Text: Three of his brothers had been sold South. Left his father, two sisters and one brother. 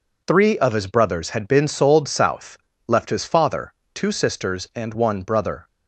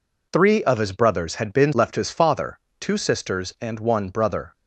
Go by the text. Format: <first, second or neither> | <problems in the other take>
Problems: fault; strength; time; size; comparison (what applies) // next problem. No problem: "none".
first | skips "sold South"; at 1.7 s